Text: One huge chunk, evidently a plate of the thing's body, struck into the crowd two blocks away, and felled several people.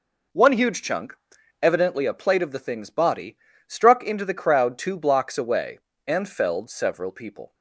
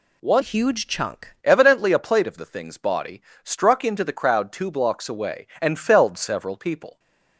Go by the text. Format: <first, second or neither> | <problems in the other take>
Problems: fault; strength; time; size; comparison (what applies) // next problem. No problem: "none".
first | changes voice from "huge" to "chunk"; from 0.4 to 1.3 s; 0.9 s long